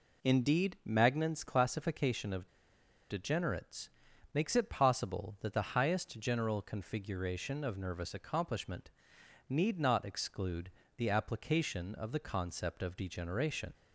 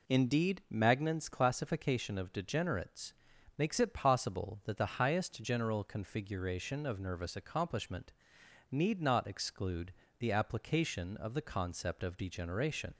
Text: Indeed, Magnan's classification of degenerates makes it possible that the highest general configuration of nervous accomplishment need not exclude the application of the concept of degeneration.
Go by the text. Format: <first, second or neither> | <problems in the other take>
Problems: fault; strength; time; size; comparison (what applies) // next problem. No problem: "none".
second | pauses between "of" and "degenerates"; noticeable; at 2.4 s; 0.63 s long // pauses between "degenerates" and "makes"; at 3.8 s; 0.44 s long; also in the second // pauses between "accomplishment" and "need"; noticeable; at 8.8 s; 0.58 s long; noticeable in the second // pauses between "exclude" and "the"; slight; at 10.7 s; 0.26 s long; slight in the second